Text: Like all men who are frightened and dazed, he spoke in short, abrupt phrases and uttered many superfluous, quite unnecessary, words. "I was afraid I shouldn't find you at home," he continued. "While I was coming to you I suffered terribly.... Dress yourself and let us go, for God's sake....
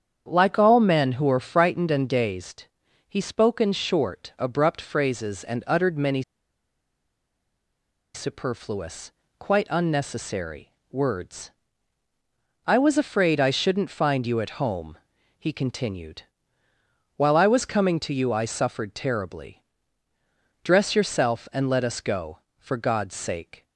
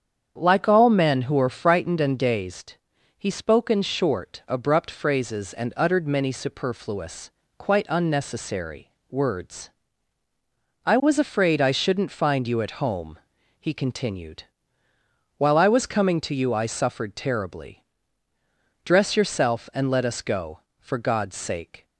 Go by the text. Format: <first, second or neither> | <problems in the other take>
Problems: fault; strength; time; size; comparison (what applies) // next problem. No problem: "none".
second | starts louder than the rest; strong; until 1.2 s; 8 dB; strong in the second // pauses between "many" and "superfluous"; strong; at 6.2 s; 1.9 s long